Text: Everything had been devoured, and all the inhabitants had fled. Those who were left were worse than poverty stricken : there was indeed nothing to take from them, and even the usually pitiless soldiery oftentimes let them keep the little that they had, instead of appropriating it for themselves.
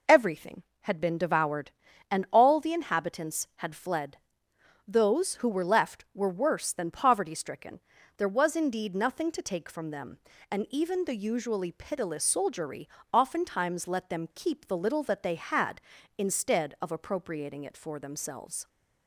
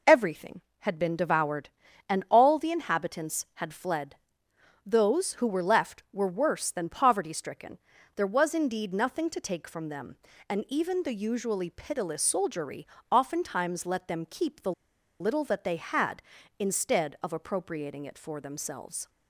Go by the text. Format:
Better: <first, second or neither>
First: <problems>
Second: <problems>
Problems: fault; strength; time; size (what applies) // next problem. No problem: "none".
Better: first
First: pauses between "soldiery" and "oftentimes"; slight; at 12.8 s; 0.24 s long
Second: pauses between "soldiery" and "oftentimes"; slight; at 12.8 s; 0.24 s long // pauses between "the" and "little"; noticeable; at 14.7 s; 0.48 s long